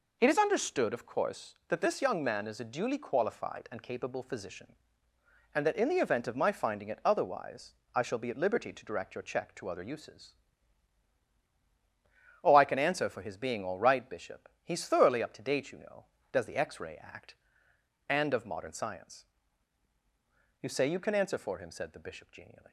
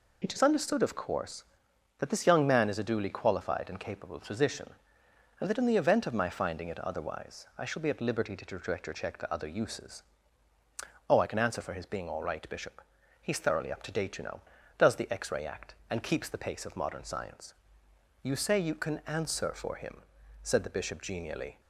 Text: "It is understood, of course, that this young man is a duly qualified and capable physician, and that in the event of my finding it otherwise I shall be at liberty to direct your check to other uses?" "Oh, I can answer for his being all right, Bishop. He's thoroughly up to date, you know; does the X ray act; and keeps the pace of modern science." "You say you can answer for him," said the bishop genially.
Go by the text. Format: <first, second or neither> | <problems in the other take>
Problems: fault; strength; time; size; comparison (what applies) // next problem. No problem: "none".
second | pauses between "otherwise" and "I"; slight; at 7.7 s; 0.20 s long // skips "keeps the pace"; at 18.3 s